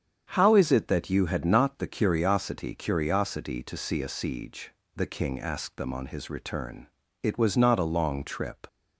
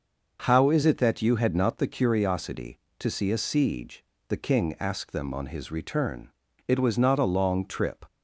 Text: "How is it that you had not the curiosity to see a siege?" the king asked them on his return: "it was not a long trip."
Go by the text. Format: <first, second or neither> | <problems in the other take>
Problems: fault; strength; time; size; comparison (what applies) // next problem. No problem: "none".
second | starts louder than the rest; strong; until 1.3 s; 8 dB // says "curiosity" twice; at 2.7 s